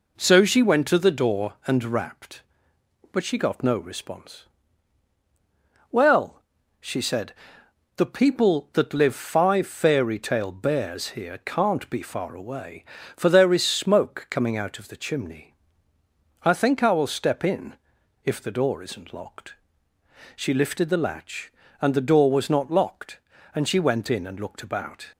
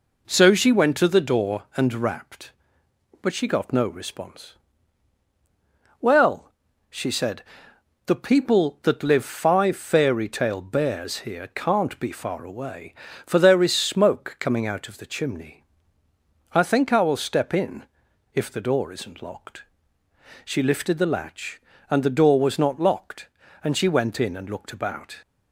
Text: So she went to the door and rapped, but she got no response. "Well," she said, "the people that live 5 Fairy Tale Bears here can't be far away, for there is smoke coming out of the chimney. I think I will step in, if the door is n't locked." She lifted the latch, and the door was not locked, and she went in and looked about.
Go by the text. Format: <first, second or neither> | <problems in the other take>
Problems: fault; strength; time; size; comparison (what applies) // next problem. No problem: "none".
neither | none